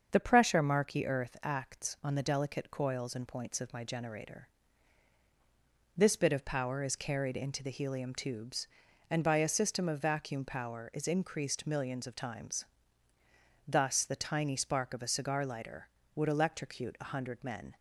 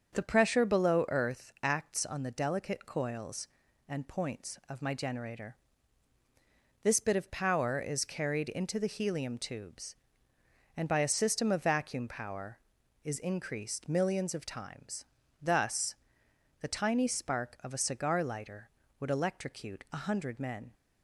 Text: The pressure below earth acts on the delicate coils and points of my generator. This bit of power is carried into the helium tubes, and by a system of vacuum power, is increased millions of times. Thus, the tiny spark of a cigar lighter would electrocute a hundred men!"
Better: second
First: starts louder than the rest; until 1.1 s; 6.5 dB // says "marky" for "below"; at 0.6 s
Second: starts louder than the rest; until 1.1 s; 7 dB

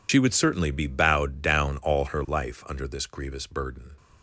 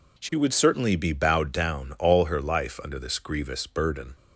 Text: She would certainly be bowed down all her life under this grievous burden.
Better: second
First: loses the start of "She"; at 0.0 s; 60 ms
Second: none

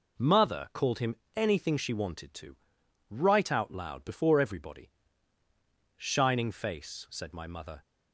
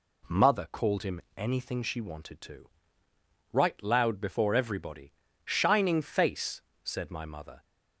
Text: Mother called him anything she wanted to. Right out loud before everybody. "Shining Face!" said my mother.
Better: first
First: pauses between "him" and "anything"; slight; at 1.1 s; 0.20 s long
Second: pauses between "him" and "anything"; slight; at 1.1 s; 0.16 s long // skips "out"; at 3.8 s

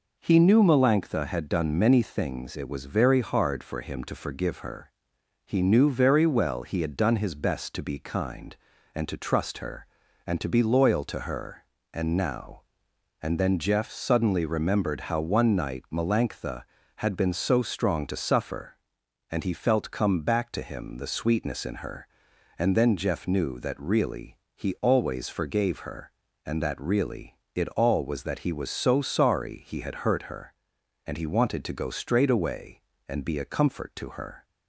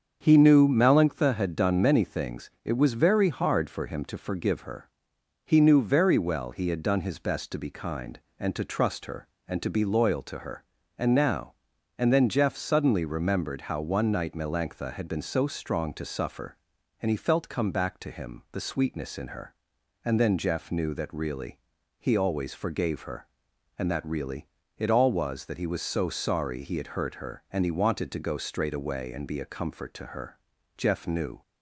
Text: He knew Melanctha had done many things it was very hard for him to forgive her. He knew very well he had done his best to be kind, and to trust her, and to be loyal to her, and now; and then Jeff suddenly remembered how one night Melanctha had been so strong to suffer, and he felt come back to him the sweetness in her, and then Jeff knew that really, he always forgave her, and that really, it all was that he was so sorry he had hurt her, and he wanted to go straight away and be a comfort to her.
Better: first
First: none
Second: starts louder than the rest; strong; until 1.2 s; 7 dB // goes on to say "Jeff knew"; noticeable; from 30.7 s on; 0.66 s long

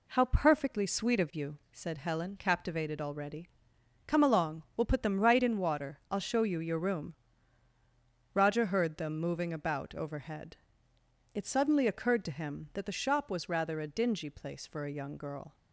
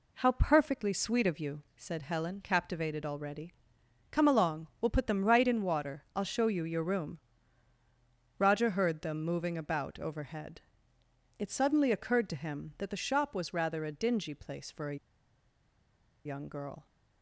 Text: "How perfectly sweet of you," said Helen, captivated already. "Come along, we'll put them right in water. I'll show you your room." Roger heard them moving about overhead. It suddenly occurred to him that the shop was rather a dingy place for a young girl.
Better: first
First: none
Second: pauses between "a" and "young"; strong; at 14.9 s; 1.2 s long

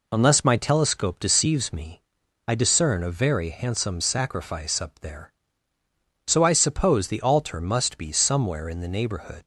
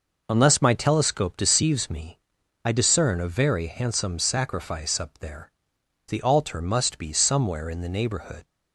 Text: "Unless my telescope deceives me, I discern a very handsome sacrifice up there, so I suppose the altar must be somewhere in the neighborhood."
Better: first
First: none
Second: skips "so I suppose"; at 5.7 s

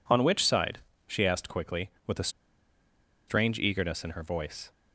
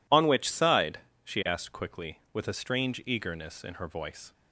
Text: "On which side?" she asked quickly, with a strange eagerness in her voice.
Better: second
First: pauses between "a" and "strange"; at 2.2 s; 0.99 s long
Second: none

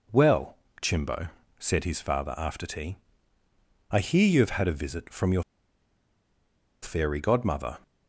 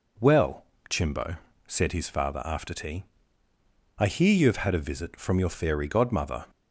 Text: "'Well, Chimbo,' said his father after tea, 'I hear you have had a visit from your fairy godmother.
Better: second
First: pauses between "your" and "fairy"; strong; at 5.4 s; 1.4 s long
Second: none

